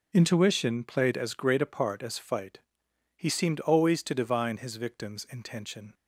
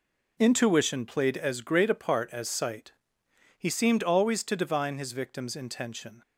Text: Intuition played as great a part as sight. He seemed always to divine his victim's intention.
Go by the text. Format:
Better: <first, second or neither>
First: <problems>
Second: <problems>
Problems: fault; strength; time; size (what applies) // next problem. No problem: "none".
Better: second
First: says "fight" for "sight"; at 2.1 s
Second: none